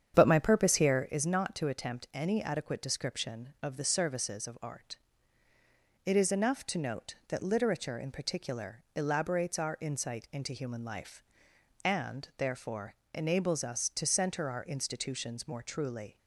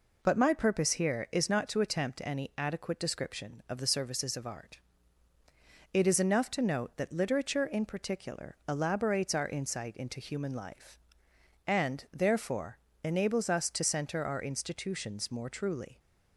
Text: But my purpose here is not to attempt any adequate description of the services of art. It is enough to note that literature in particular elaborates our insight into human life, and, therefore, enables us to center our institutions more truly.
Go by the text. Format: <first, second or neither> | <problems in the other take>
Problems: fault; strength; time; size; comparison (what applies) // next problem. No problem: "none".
second | starts louder than the rest; strong; until 1.2 s; 8.5 dB